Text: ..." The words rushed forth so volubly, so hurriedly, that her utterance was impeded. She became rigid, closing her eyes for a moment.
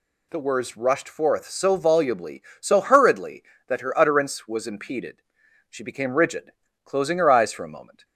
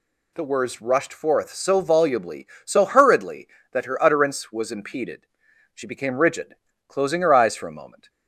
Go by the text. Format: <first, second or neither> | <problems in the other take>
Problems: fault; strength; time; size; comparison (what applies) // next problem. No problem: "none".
neither | none